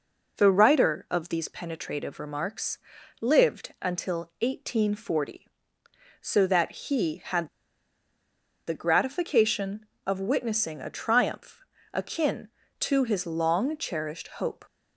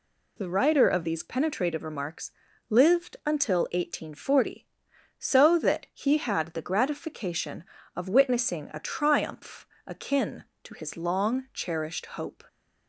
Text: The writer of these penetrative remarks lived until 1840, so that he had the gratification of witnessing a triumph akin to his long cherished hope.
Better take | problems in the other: second | pauses between "remarks" and "lived"; at 2.7 s; 0.42 s long; also in the second // pauses between "had" and "the"; at 7.4 s; 1.1 s long // pauses between "triumph" and "akin"; slight; at 11.6 s; 0.30 s long; slight in the second

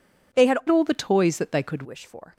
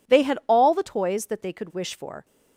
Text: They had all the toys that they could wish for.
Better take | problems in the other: second | changes voice from "all" to "could"; from 0.6 to 1.8 s; 1.2 s long

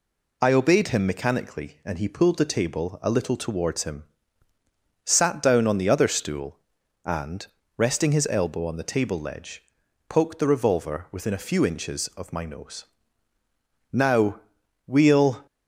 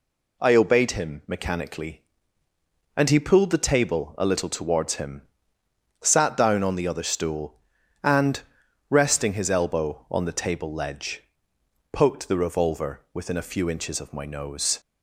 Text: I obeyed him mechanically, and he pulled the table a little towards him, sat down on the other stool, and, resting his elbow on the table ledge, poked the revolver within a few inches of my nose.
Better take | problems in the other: second | goes on to say "Now we'll"; from 13.9 s on; 1.5 s long

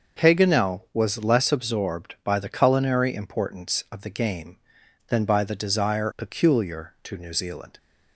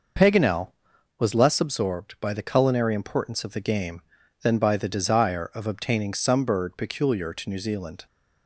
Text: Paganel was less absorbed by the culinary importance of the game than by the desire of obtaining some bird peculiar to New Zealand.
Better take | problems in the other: second | starts louder than the rest; noticeable; until 1.3 s; 6 dB // skips "of obtaining some bird"; at 6.1 s

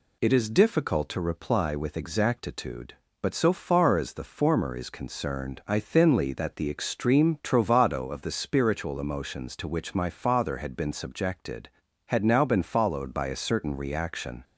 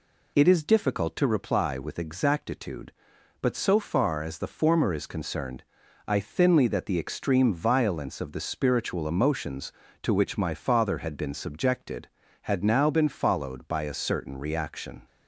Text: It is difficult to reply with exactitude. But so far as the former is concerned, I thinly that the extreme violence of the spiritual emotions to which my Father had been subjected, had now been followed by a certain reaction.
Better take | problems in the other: second | says "trovado" for "violence"; at 7.4 s

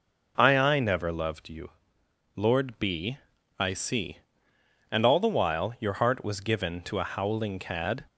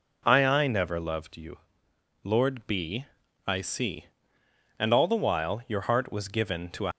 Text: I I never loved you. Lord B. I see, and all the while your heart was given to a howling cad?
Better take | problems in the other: first | stops before "howling cad"; at 6.9 s

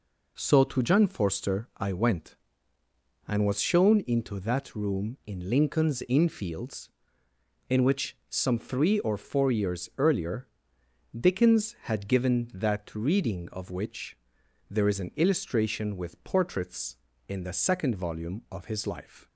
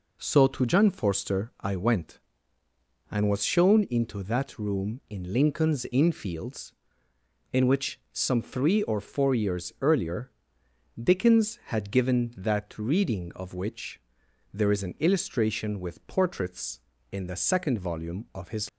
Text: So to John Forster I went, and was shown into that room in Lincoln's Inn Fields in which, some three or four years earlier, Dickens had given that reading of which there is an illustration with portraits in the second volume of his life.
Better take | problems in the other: first | pauses between "which" and "there"; noticeable; at 13.9 s; 0.54 s long; noticeable in the first // stops before "life"; at 18.6 s

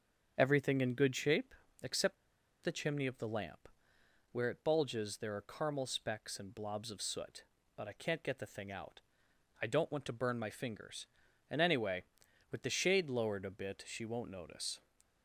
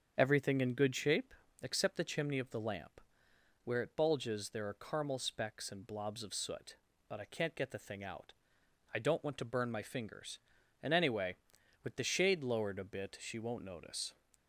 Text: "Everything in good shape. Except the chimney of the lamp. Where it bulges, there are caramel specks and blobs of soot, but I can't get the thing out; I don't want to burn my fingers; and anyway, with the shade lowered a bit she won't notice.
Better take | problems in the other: second | starts louder than the rest; strong; until 1.3 s; 7.5 dB; strong in the second // pauses between "Except" and "the"; noticeable; at 2.1 s; 0.47 s long

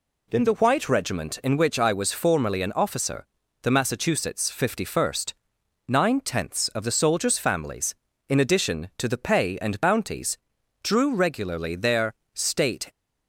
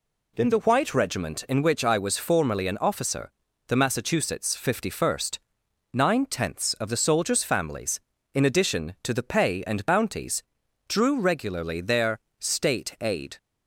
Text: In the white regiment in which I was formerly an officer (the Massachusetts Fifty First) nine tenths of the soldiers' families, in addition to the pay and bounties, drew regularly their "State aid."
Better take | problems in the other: second | pauses between "their" and "State"; slight; at 12.1 s; 0.22 s long; slight in the second // stops before "aid"; at 12.9 s

